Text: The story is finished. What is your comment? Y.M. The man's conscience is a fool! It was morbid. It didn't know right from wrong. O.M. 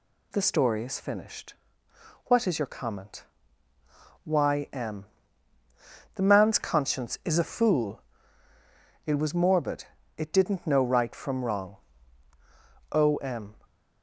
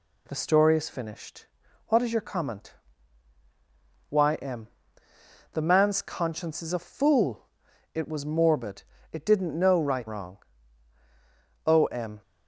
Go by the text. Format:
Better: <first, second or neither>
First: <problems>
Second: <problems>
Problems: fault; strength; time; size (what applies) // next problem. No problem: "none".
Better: first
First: none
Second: skips "from"; at 10.0 s